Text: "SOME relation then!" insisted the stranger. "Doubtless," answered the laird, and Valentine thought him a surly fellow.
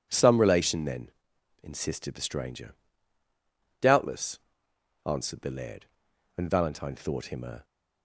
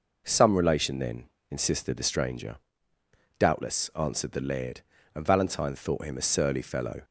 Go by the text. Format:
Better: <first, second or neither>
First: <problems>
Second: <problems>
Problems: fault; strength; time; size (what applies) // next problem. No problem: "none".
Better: second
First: stops before "surly fellow"; at 7.6 s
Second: none